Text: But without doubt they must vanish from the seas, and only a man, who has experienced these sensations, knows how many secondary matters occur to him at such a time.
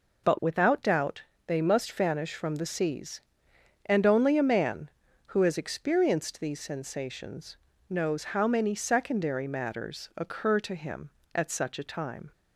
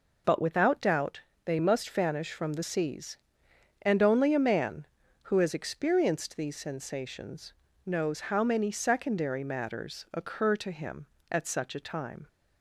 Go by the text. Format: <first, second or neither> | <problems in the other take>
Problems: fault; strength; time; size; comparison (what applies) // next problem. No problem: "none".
neither | pauses between "doubt" and "they"; slight; the same in both